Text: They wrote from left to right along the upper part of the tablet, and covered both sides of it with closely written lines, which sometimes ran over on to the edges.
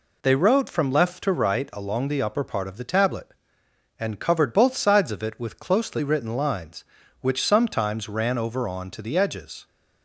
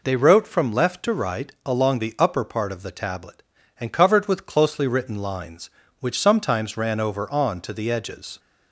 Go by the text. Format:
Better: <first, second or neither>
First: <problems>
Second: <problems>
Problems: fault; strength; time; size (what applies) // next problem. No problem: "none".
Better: first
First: none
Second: skips "both sides of it"; at 4.2 s